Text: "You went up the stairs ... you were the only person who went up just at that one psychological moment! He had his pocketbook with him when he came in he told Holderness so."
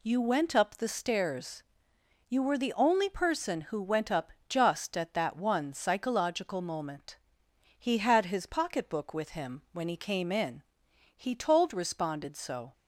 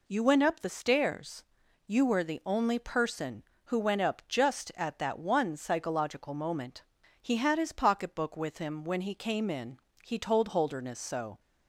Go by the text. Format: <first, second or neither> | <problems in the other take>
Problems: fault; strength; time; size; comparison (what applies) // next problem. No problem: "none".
second | pauses between "up" and "just"; slight; at 4.3 s; 0.16 s long // pauses between "in" and "he"; noticeable; at 10.6 s; 0.52 s long; slight in the second // says "Responded" for "Holderness"; at 11.7 s